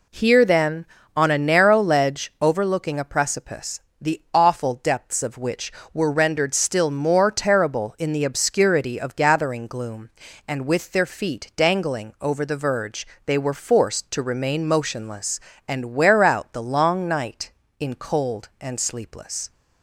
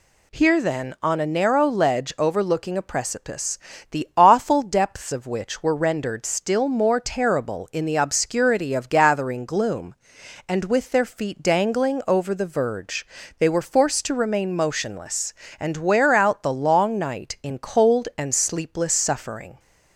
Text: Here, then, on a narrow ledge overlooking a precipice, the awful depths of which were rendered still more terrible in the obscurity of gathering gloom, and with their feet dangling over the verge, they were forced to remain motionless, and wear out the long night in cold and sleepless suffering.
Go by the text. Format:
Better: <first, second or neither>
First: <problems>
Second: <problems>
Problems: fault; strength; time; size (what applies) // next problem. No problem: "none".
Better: second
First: stops before "suffering"; at 19.5 s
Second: none